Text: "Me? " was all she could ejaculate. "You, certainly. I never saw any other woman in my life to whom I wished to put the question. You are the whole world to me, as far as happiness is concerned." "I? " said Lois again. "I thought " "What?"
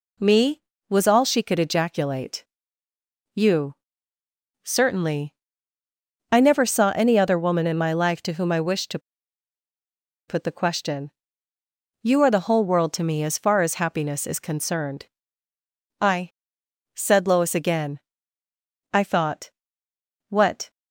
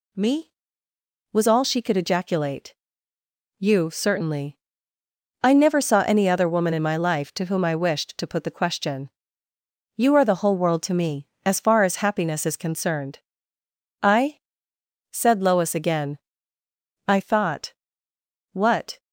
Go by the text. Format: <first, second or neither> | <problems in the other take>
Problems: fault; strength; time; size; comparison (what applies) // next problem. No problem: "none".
second | pauses between "to" and "put"; strong; at 8.9 s; 1.2 s long